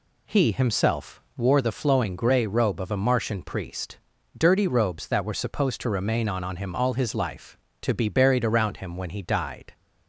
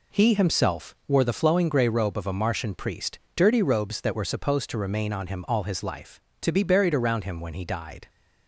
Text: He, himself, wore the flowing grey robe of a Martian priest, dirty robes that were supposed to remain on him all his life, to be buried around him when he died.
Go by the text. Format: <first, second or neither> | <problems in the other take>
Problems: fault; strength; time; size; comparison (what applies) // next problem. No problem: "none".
second | says "on" twice; at 6.4 s